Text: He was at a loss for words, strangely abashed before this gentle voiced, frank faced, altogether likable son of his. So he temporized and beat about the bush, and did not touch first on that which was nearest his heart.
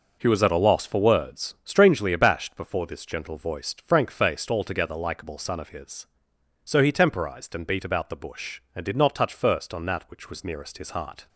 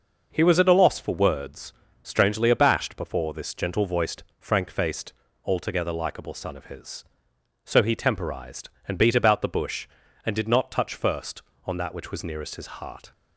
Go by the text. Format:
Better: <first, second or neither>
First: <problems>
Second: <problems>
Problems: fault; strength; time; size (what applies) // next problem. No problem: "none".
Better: neither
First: none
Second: none